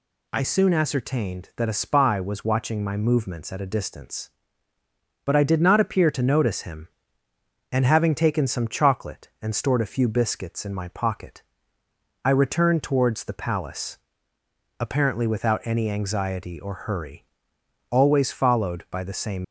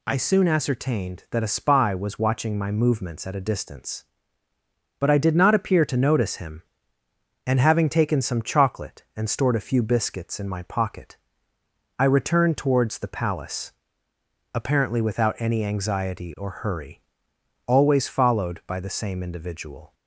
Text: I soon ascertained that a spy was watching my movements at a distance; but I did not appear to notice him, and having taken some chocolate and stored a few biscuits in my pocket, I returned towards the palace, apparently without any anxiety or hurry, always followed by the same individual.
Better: second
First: stops before "individual"; at 19.4 s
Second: none

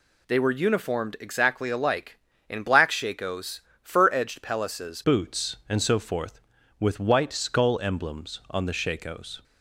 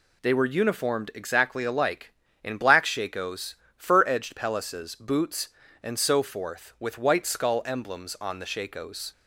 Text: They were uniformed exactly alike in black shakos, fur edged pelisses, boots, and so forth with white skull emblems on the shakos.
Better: second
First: changes voice at "boots"; from 5.0 s on; 4.4 s long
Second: none

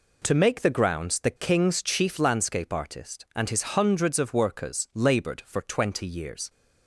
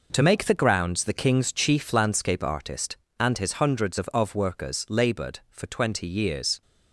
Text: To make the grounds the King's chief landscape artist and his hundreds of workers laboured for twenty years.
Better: first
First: none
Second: says "of" twice; at 4.1 s

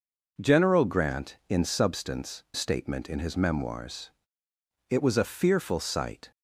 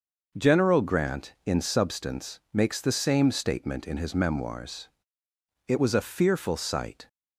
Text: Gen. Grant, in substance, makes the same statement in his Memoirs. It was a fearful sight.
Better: second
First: skips "makes the same"; at 2.4 s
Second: none

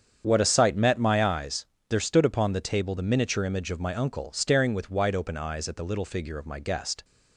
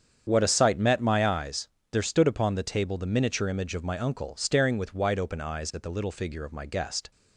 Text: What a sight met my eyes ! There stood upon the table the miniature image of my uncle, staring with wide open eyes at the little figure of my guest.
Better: neither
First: starts louder than the rest; strong; until 1.2 s; 8 dB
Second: starts louder than the rest; strong; until 1.2 s; 8 dB

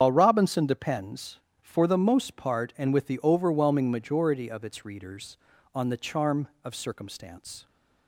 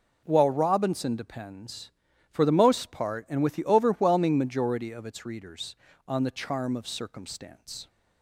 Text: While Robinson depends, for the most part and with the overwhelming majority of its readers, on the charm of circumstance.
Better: second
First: loses the start of "While"; at 0.0 s; 80 ms // starts louder than the rest; strong; until 1.0 s; 8.5 dB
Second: none

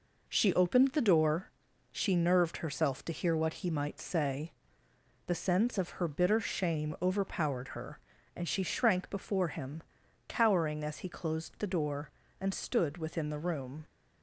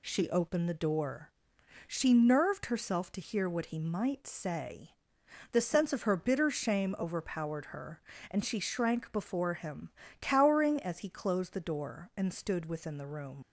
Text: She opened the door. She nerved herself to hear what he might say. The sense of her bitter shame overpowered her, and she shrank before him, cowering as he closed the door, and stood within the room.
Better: first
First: none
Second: leaves "room" unfinished; at 13.4 s; 55 ms

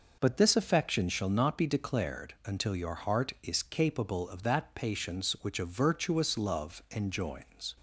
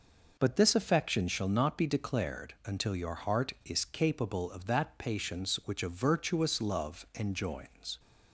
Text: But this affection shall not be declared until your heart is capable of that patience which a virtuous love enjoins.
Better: neither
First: none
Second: none

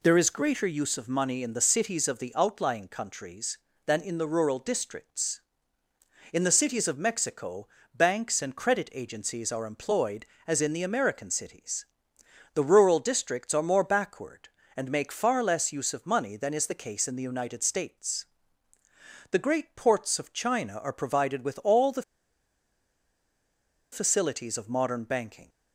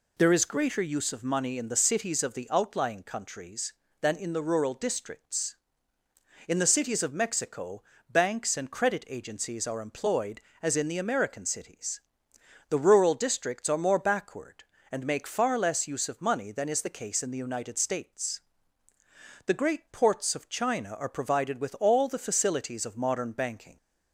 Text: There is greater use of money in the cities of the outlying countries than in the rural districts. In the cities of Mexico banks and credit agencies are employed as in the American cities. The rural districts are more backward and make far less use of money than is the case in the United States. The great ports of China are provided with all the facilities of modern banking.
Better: second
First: pauses between "Mexico" and "banks"; slight; at 7.6 s; 0.26 s long // pauses between "the" and "facilities"; strong; at 22.0 s; 1.8 s long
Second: pauses between "Mexico" and "banks"; slight; at 7.8 s; 0.26 s long

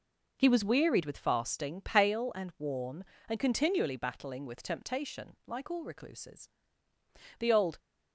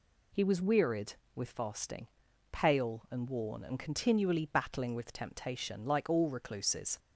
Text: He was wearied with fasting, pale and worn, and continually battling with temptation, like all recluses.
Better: second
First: goes on to say "The old"; slight; from 7.3 s on; 0.40 s long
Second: none

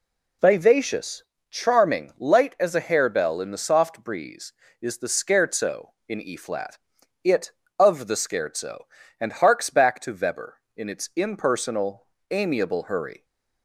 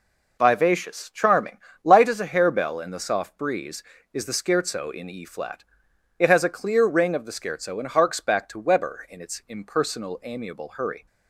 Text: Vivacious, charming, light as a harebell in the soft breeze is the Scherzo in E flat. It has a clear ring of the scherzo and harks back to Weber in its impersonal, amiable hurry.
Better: second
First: skips "has a clear ring"; at 7.6 s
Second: none

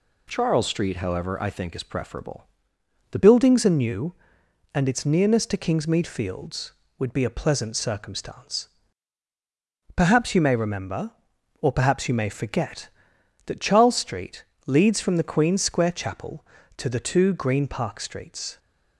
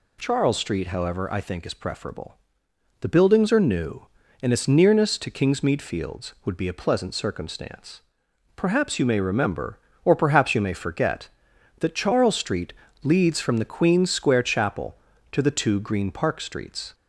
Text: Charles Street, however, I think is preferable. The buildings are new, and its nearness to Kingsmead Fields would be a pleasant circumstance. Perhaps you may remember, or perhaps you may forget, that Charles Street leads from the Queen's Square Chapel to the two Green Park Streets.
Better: second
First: changes voice at "buildings"; from 3.1 s on; 15.4 s long // pauses between "Street" and "leads"; slight; at 14.4 s; 0.22 s long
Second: pauses between "Street" and "leads"; slight; at 12.7 s; 0.32 s long

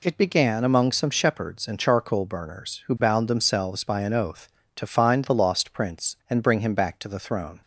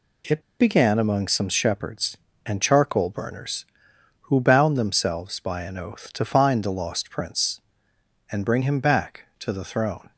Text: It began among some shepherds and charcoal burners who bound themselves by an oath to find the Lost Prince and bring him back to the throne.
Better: first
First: none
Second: pauses between "It" and "began"; slight; at 0.4 s; 0.17 s long

